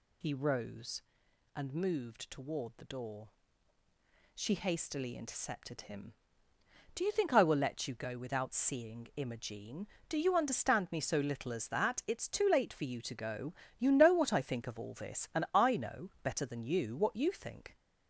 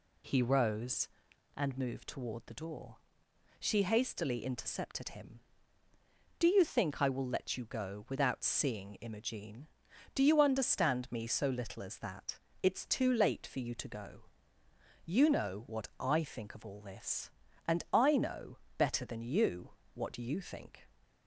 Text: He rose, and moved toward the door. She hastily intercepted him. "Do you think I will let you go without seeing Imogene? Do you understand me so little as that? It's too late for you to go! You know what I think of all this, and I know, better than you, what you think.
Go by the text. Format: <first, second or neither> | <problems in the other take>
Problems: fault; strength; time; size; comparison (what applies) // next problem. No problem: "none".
second | gets louder; slight; throughout; 3 dB